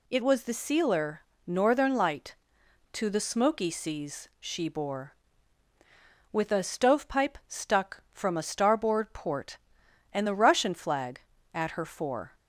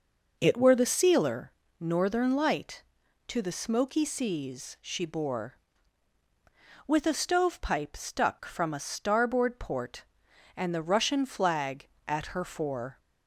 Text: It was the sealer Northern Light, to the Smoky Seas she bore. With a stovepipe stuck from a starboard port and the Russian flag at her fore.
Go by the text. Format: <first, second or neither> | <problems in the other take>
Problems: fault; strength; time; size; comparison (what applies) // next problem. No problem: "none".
first | says "were" for "was"; at 0.5 s // pauses between "sealer" and "Northern"; slight; at 1.5 s; 0.28 s long; slight in the first